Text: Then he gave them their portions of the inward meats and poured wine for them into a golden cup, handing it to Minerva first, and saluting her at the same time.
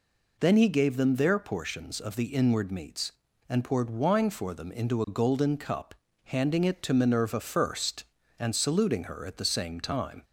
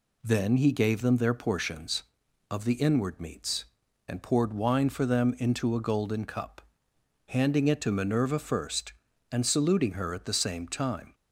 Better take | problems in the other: neither | none

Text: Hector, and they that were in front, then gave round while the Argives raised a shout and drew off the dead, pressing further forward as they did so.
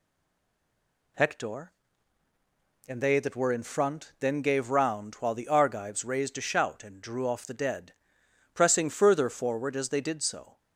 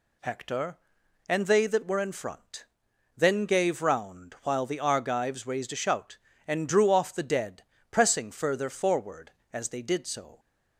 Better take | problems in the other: second | stays silent before the first word; until 1.1 s; 1.1 s long

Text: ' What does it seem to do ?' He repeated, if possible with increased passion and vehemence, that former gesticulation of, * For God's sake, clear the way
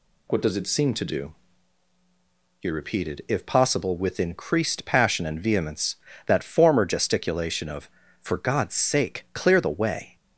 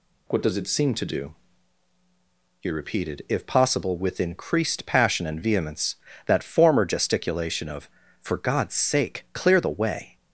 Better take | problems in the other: neither | none

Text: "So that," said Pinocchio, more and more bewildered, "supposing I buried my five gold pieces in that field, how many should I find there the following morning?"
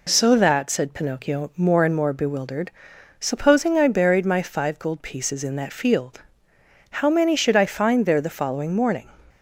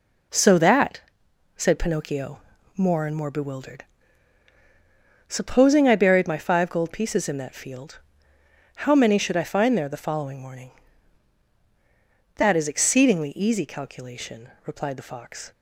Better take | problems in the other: first | goes on to say "That is exceedingly easy calculation replied the Fox"; strong; from 12.3 s on; 3.1 s long

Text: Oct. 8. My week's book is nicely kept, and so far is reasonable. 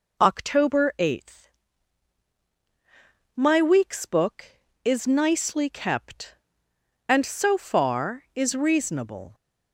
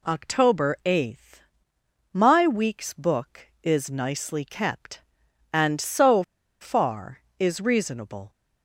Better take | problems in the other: first | pauses between "so" and "far"; at 6.2 s; 0.37 s long

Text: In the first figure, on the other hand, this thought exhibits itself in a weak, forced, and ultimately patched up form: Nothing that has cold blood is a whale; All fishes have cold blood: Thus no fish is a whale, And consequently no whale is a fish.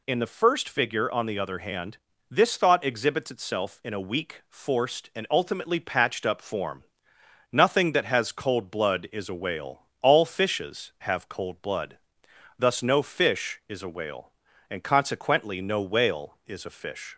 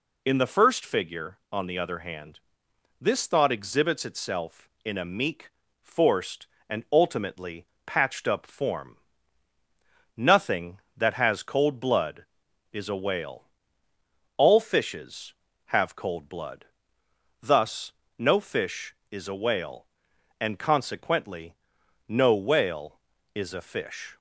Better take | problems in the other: first | says "meek" for "weak"; at 5.0 s // pauses between "ultimately" and "patched"; slight; at 7.6 s; 0.20 s long // pauses between "Thus" and "no"; slight; at 17.9 s; 0.24 s long // pauses between "consequently" and "no"; noticeable; at 21.5 s; 0.50 s long

